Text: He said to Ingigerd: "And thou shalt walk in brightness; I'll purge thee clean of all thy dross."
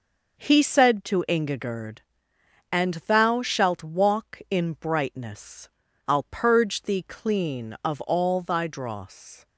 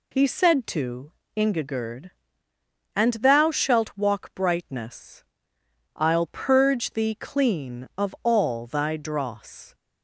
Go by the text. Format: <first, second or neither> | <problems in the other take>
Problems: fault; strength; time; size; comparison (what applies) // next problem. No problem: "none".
first | pauses between "to" and "Ingigerd"; slight; at 1.1 s; 0.24 s long // skips "in"; at 4.3 s